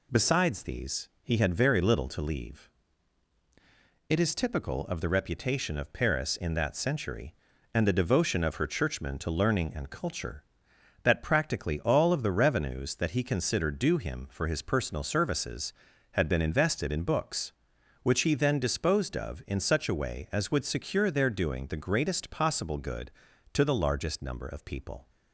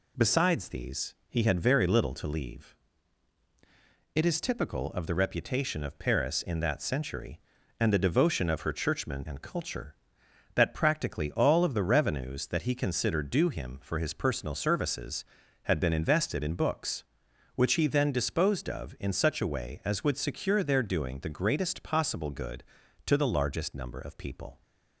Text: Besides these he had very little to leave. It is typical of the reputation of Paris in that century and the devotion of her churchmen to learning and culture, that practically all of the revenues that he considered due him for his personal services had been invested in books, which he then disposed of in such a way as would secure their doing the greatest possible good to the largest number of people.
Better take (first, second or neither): first